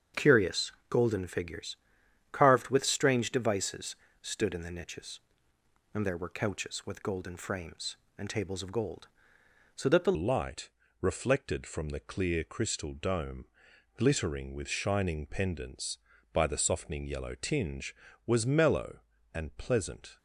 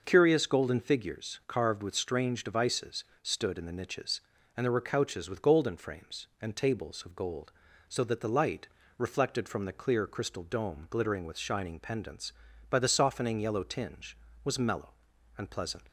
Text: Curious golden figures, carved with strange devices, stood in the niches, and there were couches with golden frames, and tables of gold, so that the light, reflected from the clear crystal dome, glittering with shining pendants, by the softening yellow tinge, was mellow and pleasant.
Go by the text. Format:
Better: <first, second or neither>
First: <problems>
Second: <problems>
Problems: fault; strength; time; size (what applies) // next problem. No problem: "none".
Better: second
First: starts louder than the rest; strong; until 1.3 s; 7.5 dB // pauses between "Curious" and "golden"; slight; at 0.7 s; 0.18 s long // changes voice at "light"; from 10.1 s on; 10.0 s long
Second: none